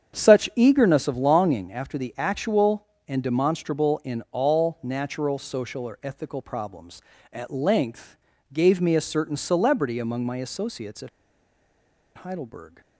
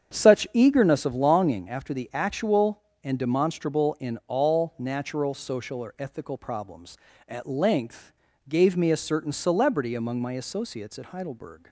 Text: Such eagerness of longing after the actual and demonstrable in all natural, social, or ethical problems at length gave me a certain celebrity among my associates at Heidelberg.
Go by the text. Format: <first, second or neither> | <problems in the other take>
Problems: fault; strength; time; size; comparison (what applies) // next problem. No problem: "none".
second | starts louder than the rest; strong; until 1.2 s; 8 dB; strong in the second // pauses between "length" and "gave"; at 8.1 s; 0.38 s long; also in the second // pauses between "at" and "Heidelberg"; at 11.0 s; 1.0 s long